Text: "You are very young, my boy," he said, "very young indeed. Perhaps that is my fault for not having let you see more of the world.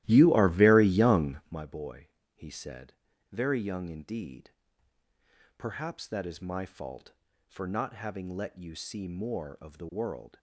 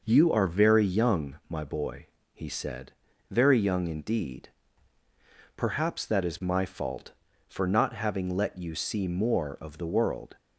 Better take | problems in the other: second | starts louder than the rest; strong; until 1.6 s; 15 dB

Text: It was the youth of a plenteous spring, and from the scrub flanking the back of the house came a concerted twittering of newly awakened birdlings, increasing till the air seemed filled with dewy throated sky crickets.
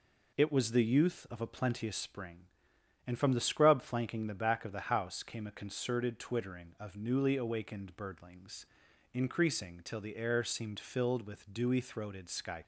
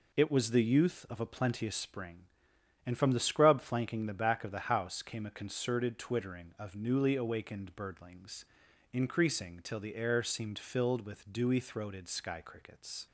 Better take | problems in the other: second | stops before "crickets"; at 12.6 s

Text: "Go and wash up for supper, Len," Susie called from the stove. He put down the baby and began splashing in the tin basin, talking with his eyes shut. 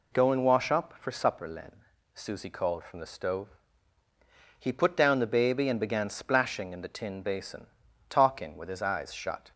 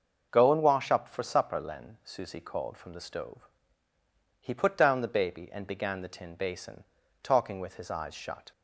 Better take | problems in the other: first | starts louder than the rest; noticeable; until 1.3 s; 6 dB // skips "splashing in"; at 6.0 s

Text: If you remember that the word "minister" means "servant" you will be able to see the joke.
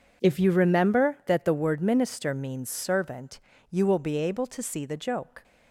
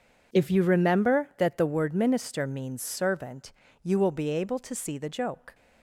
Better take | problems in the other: neither | pauses between "servant" and "you"; slight; the same in both

